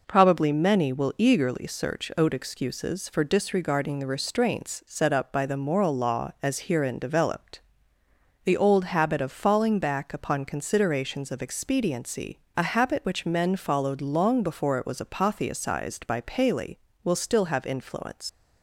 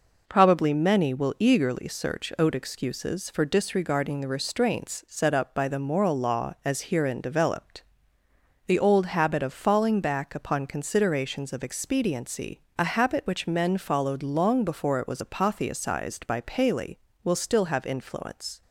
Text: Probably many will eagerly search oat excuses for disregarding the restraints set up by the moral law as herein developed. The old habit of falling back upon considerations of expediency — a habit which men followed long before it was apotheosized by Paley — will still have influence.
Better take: second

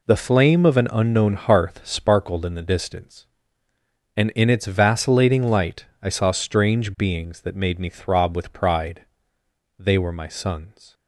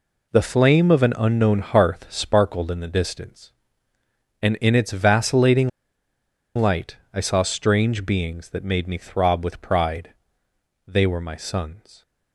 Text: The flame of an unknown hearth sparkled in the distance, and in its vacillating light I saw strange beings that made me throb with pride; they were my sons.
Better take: first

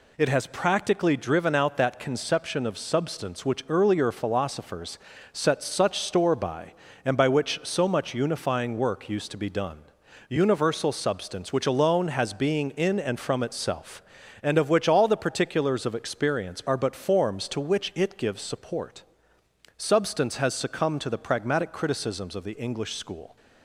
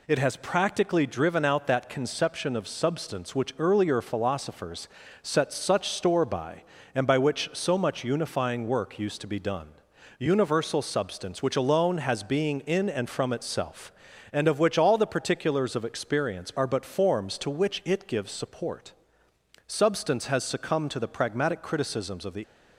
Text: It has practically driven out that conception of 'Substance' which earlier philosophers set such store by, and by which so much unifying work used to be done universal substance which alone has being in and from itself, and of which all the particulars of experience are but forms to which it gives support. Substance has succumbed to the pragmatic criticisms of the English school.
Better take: first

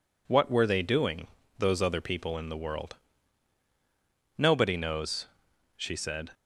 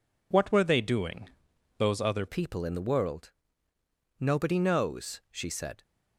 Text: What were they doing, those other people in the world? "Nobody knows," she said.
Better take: first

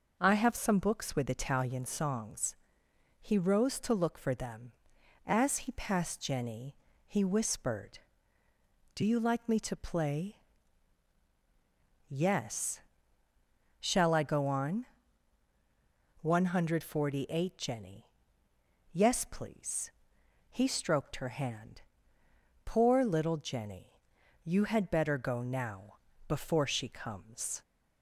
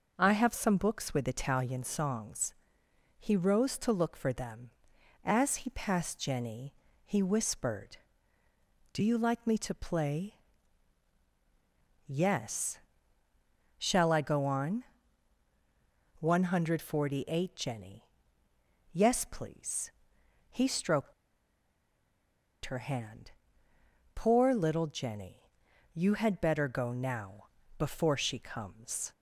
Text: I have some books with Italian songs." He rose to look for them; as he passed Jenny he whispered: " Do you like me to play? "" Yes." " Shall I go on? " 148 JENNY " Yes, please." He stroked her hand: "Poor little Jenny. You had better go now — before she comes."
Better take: first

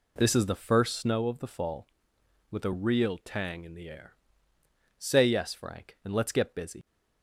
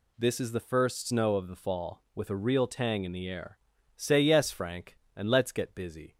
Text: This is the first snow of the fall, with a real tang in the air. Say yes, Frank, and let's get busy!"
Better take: second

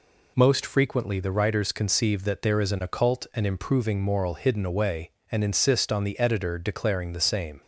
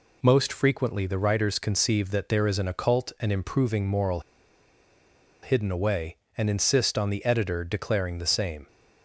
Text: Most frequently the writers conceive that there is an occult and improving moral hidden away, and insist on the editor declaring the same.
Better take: first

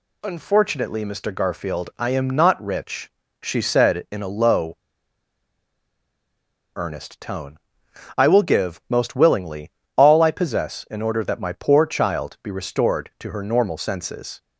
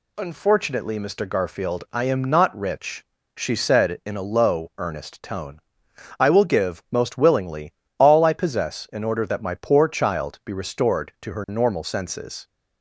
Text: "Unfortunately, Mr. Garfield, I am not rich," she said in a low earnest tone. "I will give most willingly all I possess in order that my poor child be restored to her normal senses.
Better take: second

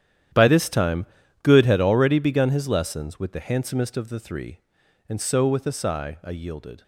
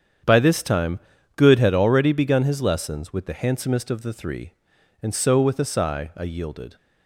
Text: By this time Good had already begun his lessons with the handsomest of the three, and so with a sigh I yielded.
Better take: second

